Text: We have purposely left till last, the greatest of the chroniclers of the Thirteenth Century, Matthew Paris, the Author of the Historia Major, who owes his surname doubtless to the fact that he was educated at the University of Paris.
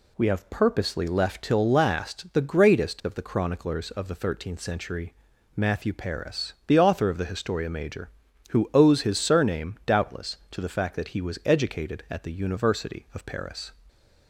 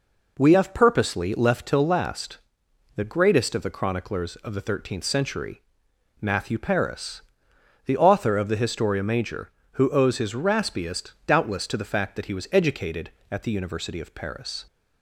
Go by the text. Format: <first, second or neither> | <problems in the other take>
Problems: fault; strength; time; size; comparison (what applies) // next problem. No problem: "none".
first | says "raspiest" for "surname"; at 10.3 s